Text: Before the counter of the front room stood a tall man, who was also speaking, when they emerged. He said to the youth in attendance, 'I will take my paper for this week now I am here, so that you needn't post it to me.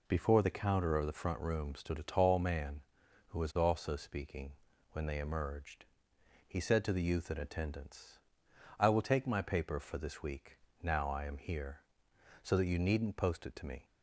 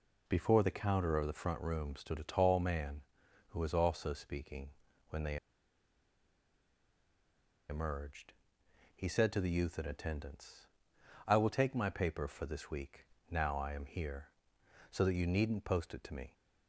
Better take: first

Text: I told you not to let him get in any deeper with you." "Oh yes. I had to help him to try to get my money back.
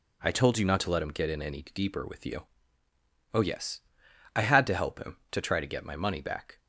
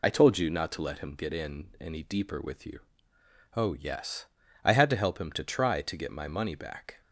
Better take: first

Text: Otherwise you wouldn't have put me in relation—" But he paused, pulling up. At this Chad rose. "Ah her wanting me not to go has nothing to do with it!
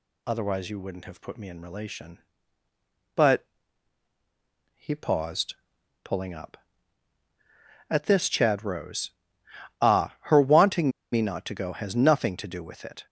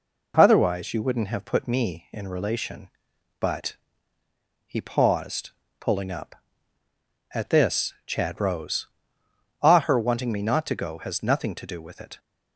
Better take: second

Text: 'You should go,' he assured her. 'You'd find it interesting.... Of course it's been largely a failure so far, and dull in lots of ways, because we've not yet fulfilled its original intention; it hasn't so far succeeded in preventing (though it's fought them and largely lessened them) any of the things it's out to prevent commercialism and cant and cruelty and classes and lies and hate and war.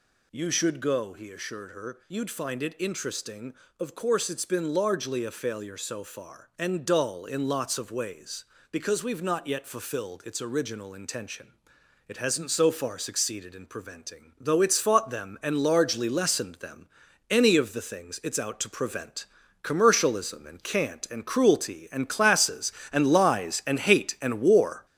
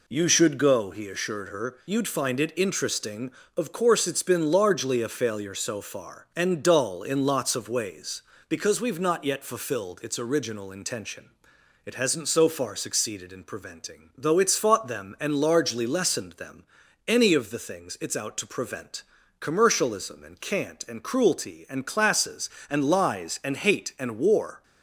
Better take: second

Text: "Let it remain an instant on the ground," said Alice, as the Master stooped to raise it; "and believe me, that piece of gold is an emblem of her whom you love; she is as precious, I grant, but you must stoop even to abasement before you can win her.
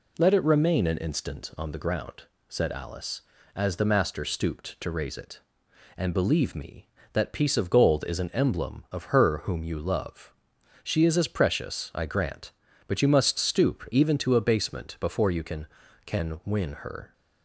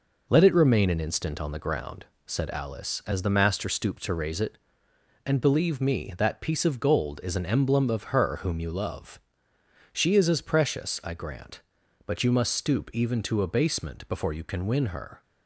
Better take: second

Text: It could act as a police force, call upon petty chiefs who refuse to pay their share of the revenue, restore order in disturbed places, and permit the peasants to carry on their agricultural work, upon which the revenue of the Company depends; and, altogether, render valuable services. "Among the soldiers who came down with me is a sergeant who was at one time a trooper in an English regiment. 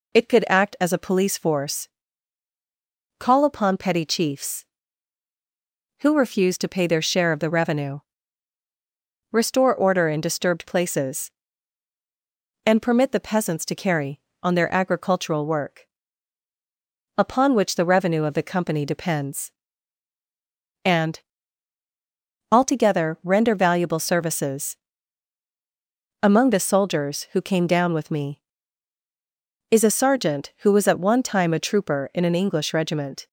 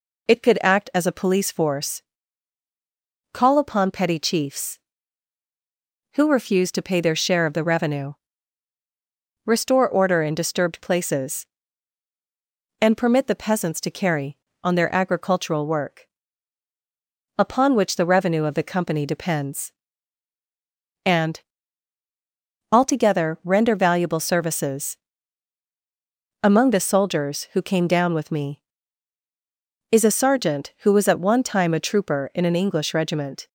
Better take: neither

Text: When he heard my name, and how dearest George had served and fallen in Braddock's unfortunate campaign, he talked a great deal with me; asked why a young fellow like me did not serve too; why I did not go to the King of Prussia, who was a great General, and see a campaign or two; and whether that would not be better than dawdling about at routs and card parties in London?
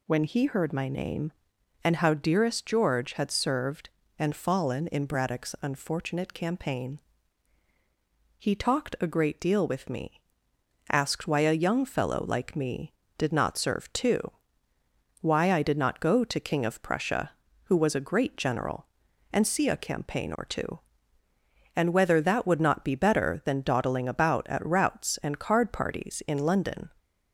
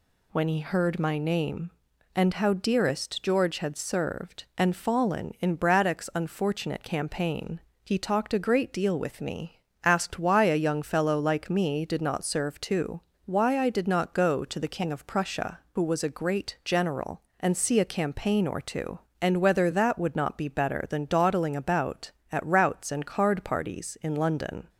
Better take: second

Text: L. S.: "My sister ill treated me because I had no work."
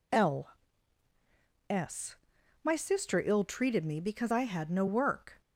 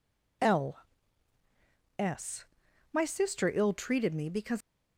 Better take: first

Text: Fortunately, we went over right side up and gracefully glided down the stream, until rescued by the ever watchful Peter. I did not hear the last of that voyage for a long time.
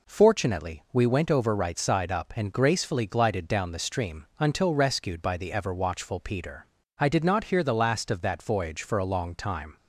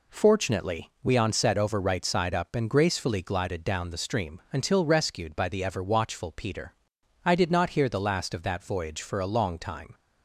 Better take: first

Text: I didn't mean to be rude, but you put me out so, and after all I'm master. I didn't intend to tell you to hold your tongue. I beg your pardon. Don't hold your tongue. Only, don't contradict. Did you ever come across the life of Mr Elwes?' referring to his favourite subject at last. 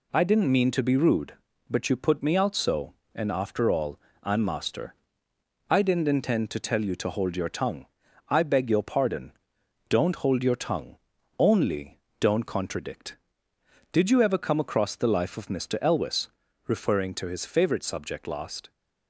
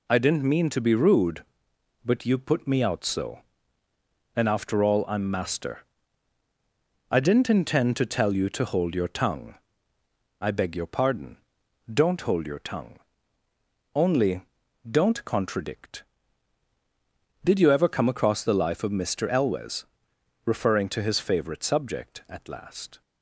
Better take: second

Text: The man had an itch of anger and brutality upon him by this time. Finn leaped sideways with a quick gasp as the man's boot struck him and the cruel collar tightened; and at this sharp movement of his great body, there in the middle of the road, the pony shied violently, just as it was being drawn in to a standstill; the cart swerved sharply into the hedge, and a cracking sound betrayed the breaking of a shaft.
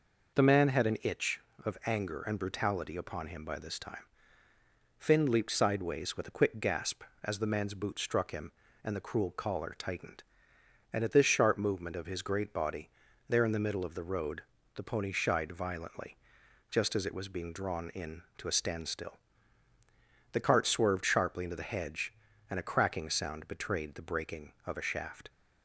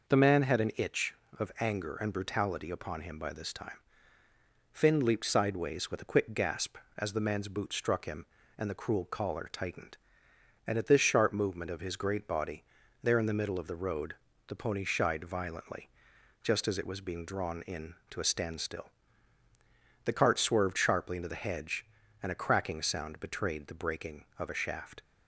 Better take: neither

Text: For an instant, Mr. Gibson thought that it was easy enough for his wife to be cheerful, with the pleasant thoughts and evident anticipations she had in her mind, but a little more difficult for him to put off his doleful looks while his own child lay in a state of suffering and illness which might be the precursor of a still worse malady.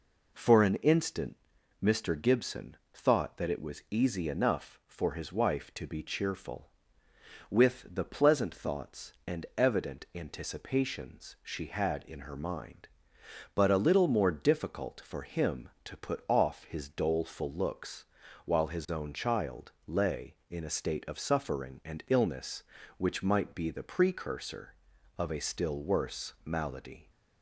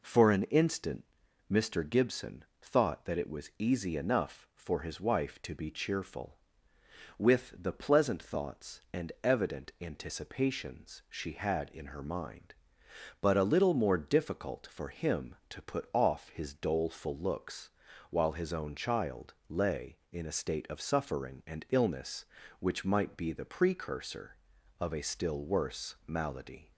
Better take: neither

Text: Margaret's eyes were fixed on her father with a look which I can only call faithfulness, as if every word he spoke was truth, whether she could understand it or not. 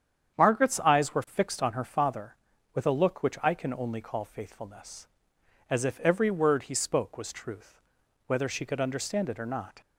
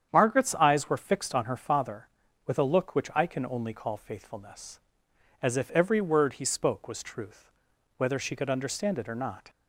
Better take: neither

